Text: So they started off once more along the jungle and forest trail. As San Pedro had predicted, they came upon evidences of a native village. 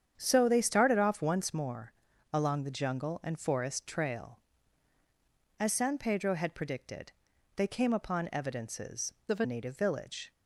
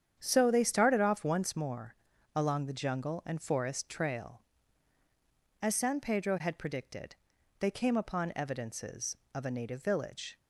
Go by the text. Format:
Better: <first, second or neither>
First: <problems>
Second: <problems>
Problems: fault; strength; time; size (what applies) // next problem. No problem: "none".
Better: second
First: starts louder than the rest; strong; until 1.1 s; 8.5 dB // pauses between "more" and "along"; at 1.9 s; 0.42 s long // changes voice from "of" to "a"; from 9.2 to 9.4 s; 0.2 s long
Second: starts louder than the rest; strong; until 1.2 s; 8.5 dB // pauses between "more" and "along"; at 1.9 s; 0.42 s long